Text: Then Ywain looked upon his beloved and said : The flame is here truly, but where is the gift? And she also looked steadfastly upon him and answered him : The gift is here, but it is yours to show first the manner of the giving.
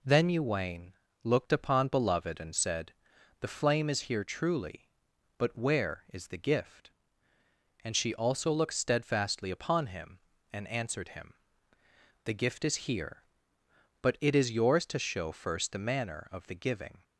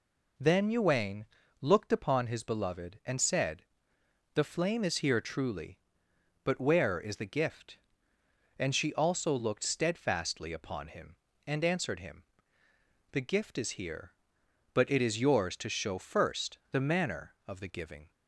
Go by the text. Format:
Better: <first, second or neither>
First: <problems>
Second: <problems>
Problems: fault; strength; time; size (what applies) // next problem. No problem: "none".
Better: second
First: pauses between "Ywain" and "looked"; slight; at 0.9 s; 0.30 s long // skips "his"; at 1.8 s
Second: pauses between "Ywain" and "looked"; slight; at 1.2 s; 0.36 s long